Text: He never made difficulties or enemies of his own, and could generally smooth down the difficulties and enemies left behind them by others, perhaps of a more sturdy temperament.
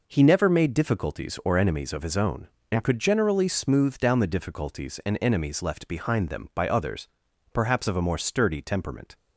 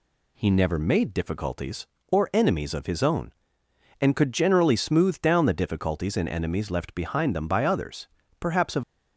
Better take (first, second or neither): first